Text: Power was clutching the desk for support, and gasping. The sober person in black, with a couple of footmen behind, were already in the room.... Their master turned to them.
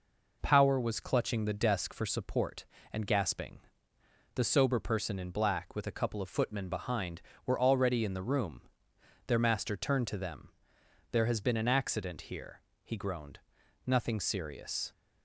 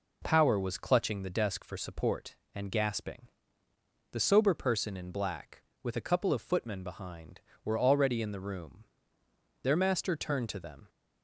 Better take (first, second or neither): second